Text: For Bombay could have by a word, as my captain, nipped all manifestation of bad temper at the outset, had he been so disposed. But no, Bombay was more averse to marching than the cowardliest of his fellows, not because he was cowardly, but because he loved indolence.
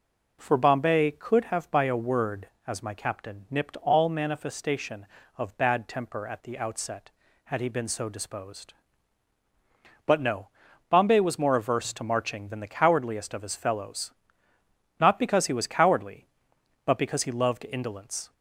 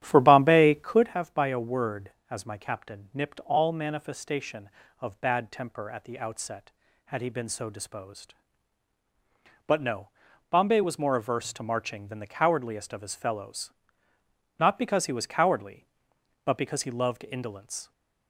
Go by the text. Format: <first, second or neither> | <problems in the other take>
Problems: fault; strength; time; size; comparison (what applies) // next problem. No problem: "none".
first | starts louder than the rest; strong; until 1.2 s; 11.5 dB